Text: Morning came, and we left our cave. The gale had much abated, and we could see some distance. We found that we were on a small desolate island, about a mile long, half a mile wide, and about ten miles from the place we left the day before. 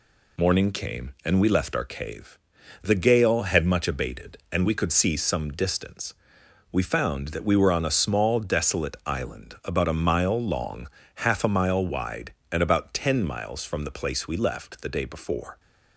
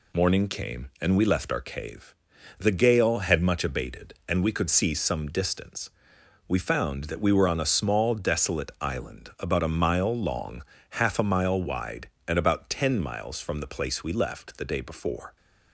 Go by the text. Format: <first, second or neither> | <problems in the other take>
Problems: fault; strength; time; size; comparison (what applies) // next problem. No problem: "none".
neither | none